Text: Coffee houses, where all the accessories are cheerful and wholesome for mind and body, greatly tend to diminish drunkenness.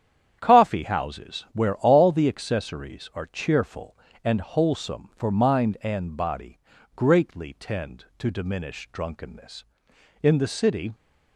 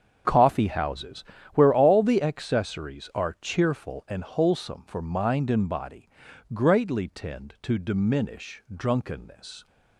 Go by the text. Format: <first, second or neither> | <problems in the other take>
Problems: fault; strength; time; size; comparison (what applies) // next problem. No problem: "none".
second | starts louder than the rest; strong; until 1.4 s; 9 dB; strong in the second // goes on to say "In the city"; noticeable; from 10.2 s on; 0.70 s long